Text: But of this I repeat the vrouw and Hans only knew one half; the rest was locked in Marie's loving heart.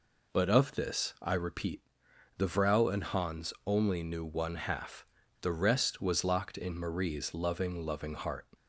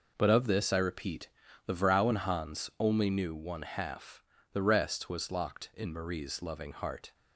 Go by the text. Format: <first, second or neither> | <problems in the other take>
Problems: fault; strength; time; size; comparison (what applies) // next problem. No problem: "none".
second | pauses between "repeat" and "the"; noticeable; at 1.7 s; 0.58 s long; slight in the second // says "loving" twice; at 7.8 s